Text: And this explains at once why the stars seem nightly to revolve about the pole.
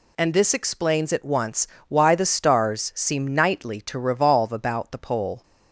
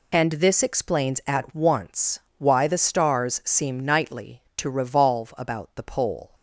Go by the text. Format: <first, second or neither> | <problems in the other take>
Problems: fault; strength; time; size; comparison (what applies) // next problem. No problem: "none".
neither | pauses between "once" and "why"; slight; the same in both